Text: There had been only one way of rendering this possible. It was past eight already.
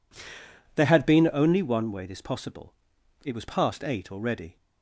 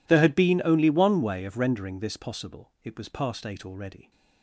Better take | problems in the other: second | skips "of rendering"; at 2.0 s

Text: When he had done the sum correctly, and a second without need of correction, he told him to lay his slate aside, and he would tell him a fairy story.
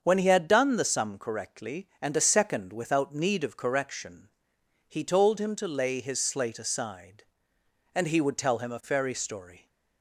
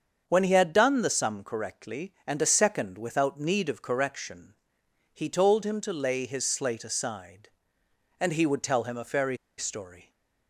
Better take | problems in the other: first | starts louder than the rest; until 1.2 s; 7 dB; also in the first // pauses between "fairy" and "story"; slight; at 9.3 s; 0.21 s long

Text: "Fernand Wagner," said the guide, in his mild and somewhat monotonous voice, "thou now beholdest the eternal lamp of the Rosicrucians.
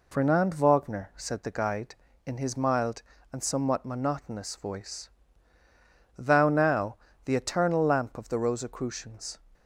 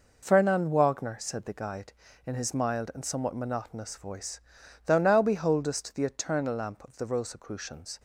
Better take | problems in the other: second | skips "beholdest"; at 7.1 s

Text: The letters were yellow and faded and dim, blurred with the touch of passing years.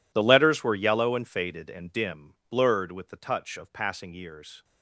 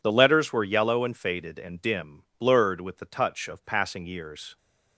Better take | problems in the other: second | gets quieter; strong; throughout; 20 dB

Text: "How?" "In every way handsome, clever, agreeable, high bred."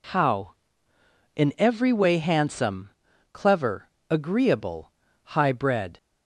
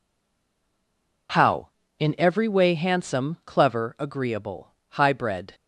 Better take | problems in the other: first | stays silent before the first word; noticeable; until 1.2 s; 1.2 s long

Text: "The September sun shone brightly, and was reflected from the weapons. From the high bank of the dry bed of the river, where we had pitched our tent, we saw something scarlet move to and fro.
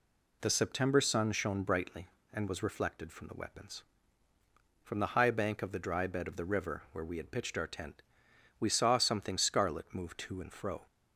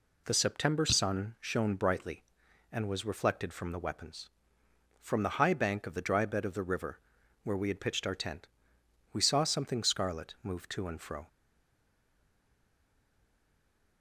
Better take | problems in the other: first | stays silent after the last word; strong; from 11.2 s on; 2.8 s long

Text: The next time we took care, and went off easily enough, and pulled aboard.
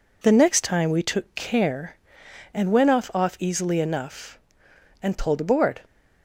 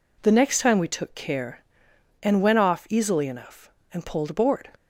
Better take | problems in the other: second | says "off" twice; at 3.1 s

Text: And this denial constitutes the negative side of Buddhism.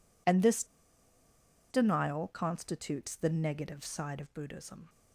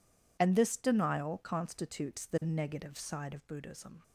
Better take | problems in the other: second | pauses between "this" and "denial"; at 0.6 s; 1.0 s long

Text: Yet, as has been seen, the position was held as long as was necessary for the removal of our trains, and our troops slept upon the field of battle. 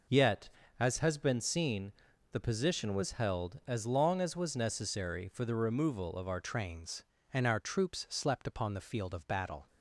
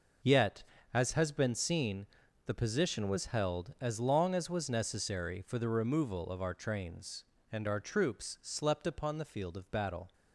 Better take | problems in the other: second | changes voice at "trains"; from 6.4 s on; 3.2 s long

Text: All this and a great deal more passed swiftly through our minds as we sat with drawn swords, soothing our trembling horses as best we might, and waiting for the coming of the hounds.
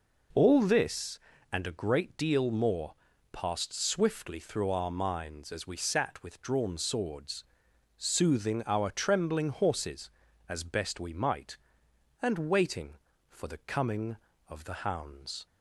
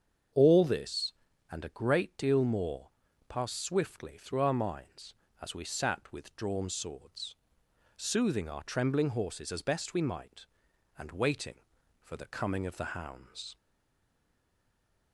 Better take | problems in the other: first | starts louder than the rest; strong; until 1.7 s; 7 dB // pauses between "more" and "passed"; at 2.8 s; 0.40 s long; also in the first // stays silent after the last word; noticeable; from 13.5 s on; 1.6 s long

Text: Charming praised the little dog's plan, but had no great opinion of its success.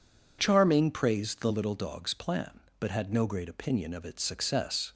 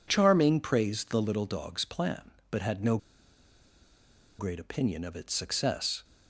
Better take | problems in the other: first | pauses between "no" and "great"; strong; at 2.9 s; 1.4 s long

